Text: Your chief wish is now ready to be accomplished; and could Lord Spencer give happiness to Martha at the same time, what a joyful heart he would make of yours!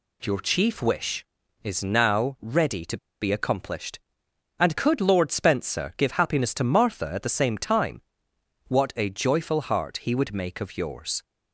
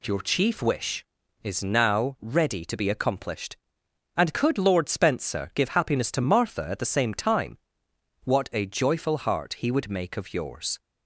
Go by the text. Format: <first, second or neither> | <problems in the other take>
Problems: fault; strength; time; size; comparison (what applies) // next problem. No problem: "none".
second | pauses between "to" and "be"; slight; at 2.9 s; 0.25 s long